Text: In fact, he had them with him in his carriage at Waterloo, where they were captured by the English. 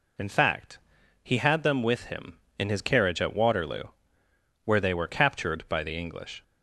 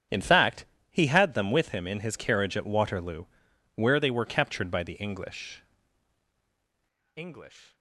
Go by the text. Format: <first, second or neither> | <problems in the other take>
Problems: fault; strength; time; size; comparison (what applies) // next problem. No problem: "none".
first | starts louder than the rest; strong; until 1.3 s; 8 dB // says "English" twice; at 7.1 s